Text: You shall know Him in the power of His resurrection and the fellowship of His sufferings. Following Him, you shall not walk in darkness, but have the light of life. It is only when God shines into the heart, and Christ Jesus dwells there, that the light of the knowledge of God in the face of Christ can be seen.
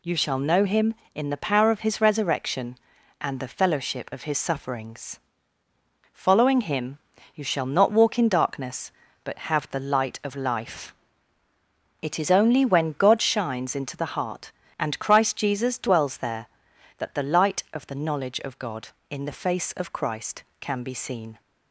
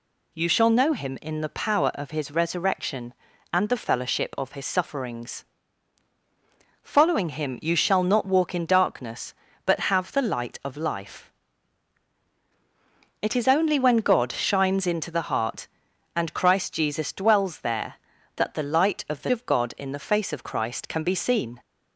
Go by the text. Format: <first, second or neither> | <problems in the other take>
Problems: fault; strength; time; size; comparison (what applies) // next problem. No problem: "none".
first | skips "knowledge"; at 19.3 s